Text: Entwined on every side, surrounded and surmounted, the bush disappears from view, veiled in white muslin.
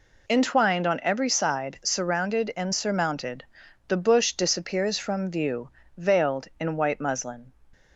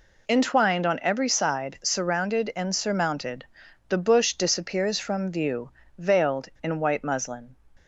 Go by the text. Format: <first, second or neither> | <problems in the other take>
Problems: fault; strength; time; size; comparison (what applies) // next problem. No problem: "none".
neither | none